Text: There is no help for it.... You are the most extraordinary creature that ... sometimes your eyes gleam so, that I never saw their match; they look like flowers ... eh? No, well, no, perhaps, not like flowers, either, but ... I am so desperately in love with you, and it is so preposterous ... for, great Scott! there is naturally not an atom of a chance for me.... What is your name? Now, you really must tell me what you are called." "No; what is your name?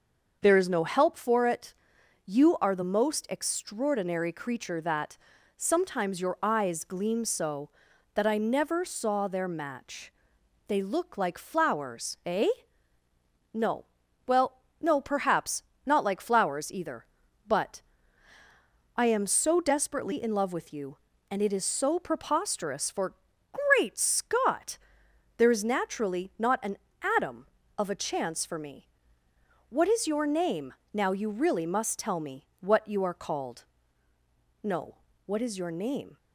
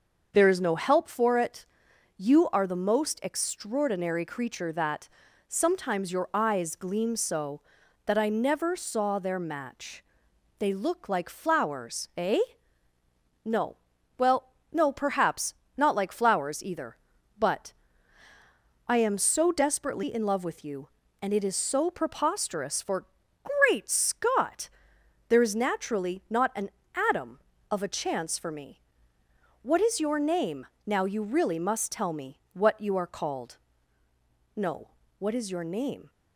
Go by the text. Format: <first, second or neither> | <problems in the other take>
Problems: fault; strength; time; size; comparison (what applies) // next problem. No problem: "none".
neither | starts louder than the rest; the same in both // pauses between "an" and "atom"; the same in both